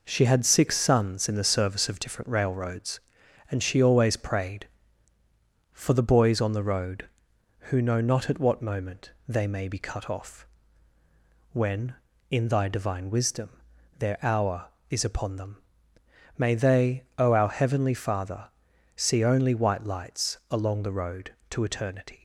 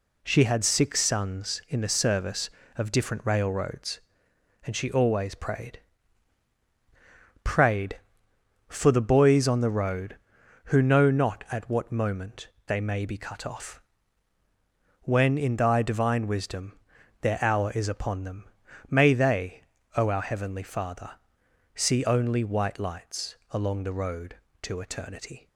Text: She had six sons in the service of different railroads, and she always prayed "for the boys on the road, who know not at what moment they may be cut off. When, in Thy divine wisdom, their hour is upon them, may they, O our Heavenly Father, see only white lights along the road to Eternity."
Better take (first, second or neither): first